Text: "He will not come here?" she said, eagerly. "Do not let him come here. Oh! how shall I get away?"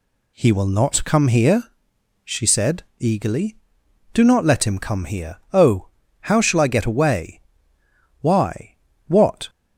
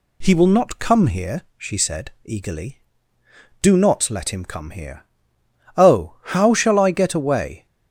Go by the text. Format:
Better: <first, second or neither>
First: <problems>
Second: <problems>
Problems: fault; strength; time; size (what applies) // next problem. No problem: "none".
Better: second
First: goes on to say "Why what"; noticeable; from 8.2 s on; 1.2 s long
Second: none